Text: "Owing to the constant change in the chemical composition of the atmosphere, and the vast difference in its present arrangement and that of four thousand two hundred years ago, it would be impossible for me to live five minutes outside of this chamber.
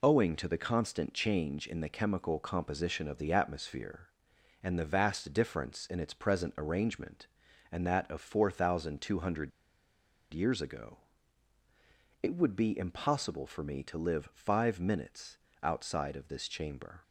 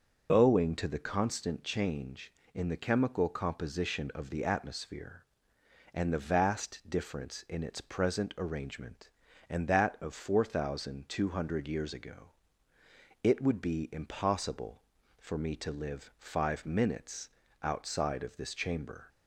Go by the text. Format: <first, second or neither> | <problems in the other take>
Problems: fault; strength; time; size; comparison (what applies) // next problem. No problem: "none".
second | pauses between "hundred" and "years"; noticeable; at 9.5 s; 0.83 s long // pauses between "minutes" and "outside"; slight; at 15.3 s; 0.26 s long; slight in the second